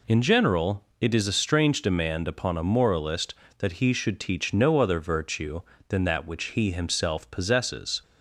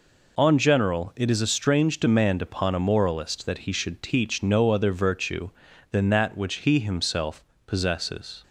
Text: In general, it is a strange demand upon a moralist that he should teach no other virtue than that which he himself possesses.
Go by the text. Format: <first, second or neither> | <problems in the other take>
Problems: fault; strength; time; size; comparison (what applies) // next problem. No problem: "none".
first | says "On" for "In"; at 0.3 s // pauses between "himself" and "possesses"; slight; at 7.4 s; 0.22 s long